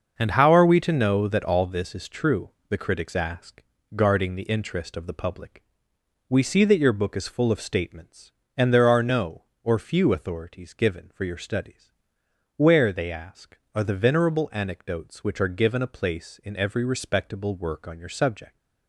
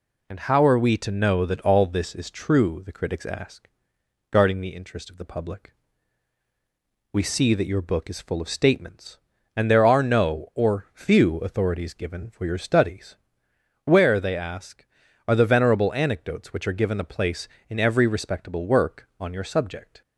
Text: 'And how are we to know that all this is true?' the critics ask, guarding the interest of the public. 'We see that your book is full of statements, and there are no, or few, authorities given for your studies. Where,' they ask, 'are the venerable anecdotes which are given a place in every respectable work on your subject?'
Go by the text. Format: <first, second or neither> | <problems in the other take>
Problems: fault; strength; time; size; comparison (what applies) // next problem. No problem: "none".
second | starts louder than the rest; until 1.9 s; 6.5 dB